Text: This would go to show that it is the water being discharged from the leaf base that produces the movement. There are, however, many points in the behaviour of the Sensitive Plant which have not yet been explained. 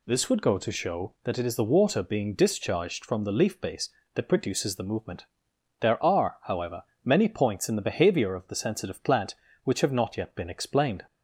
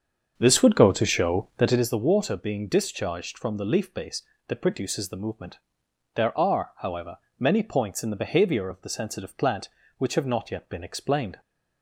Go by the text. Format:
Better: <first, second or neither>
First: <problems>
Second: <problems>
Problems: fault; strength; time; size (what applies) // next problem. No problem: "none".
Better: first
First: none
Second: starts louder than the rest; until 2.0 s; 7 dB